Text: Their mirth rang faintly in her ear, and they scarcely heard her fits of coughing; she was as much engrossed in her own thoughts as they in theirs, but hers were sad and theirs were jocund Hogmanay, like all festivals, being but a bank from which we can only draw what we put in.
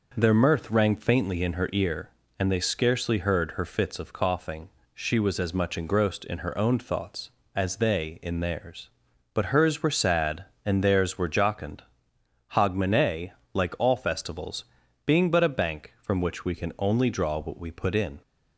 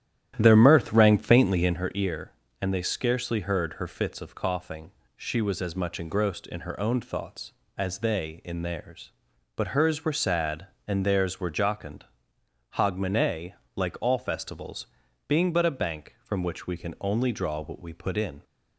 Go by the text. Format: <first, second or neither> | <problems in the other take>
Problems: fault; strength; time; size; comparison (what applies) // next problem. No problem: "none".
first | starts louder than the rest; strong; until 1.8 s; 11.5 dB // pauses between "jocund" and "Hogmanay"; noticeable; at 12.0 s; 0.66 s long; noticeable in the first